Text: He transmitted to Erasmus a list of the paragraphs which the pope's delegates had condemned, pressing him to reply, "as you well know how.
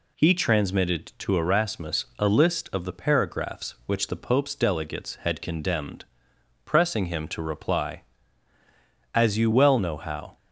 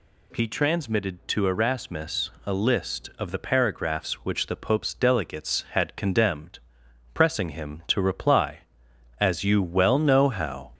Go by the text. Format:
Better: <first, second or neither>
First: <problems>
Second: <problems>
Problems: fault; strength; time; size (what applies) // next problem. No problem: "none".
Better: first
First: none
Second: gets louder; slight; throughout; 3 dB // pauses between "Erasmus" and "a"; slight; at 2.3 s; 0.16 s long